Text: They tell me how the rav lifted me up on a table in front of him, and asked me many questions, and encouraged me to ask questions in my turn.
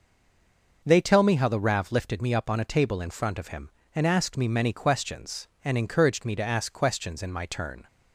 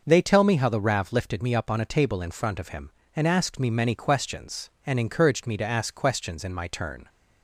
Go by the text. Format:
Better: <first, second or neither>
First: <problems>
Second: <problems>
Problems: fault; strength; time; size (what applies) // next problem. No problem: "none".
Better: second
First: stays silent before the first word; slight; until 0.8 s; 0.8 s long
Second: none